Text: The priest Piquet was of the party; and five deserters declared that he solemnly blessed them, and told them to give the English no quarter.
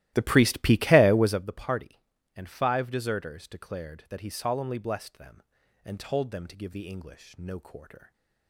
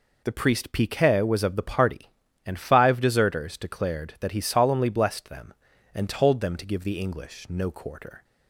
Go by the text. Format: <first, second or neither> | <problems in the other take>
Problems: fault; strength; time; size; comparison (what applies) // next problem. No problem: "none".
second | starts louder than the rest; strong; until 1.4 s; 15.5 dB